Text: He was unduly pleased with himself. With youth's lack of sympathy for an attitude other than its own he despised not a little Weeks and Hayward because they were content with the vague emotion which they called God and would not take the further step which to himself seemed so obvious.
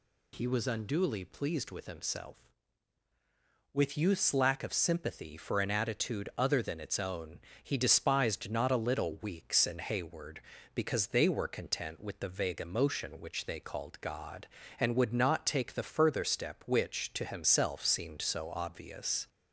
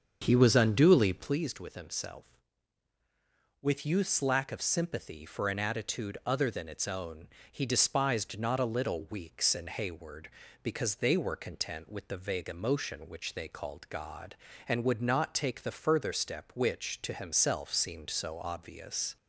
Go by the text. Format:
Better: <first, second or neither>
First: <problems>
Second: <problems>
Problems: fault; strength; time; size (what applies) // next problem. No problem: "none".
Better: first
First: pauses between "own" and "he"; slight; at 7.3 s; 0.24 s long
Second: starts louder than the rest; until 1.4 s; 7 dB // pauses between "own" and "he"; slight; at 7.2 s; 0.24 s long